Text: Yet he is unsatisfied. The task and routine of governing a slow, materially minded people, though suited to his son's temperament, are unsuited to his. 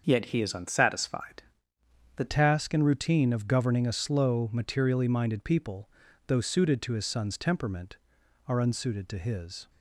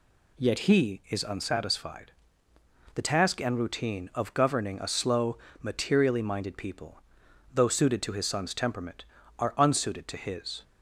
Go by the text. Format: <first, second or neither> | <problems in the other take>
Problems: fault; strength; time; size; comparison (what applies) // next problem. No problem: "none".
second | starts louder than the rest; until 1.0 s; 6.5 dB // changes voice at "task"; from 2.2 s on; 7.4 s long